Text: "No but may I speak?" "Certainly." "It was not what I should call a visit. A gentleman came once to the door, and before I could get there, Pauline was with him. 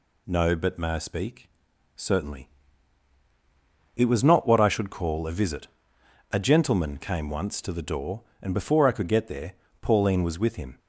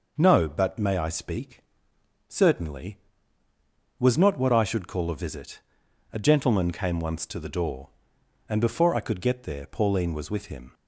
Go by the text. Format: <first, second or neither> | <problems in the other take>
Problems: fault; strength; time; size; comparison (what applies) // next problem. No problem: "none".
first | skips "It"; at 3.4 s